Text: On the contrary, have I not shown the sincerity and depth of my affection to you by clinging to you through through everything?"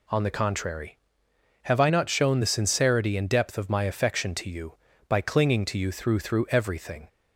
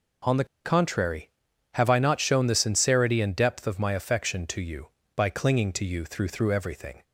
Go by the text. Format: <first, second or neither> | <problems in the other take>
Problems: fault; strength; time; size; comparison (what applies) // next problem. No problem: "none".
first | pauses between "the" and "contrary"; slight; at 0.4 s; 0.19 s long